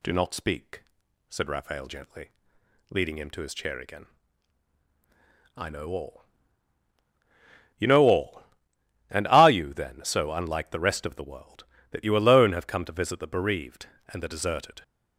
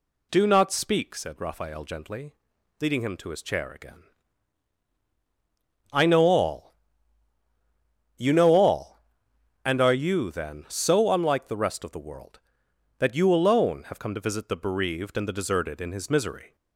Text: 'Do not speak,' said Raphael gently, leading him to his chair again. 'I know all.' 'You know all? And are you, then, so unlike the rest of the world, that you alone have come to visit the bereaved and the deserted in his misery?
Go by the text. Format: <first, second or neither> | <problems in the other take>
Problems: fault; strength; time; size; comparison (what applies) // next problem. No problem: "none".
second | stops before "in his misery"; at 14.8 s